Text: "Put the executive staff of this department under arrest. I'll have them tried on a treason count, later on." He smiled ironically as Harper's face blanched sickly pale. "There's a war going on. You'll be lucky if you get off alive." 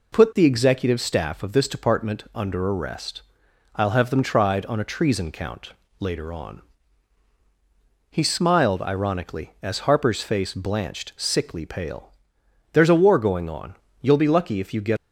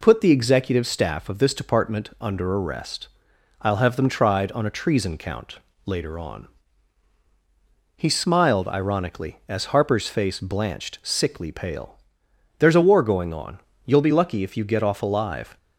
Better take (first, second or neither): second